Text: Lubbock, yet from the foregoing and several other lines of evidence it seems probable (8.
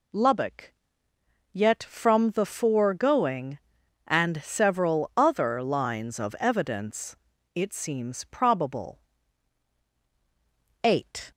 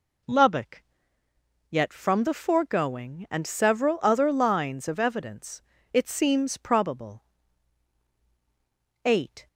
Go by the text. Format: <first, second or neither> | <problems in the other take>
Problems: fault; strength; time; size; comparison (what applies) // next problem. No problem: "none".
neither | pauses between "evidence" and "it"; the same in both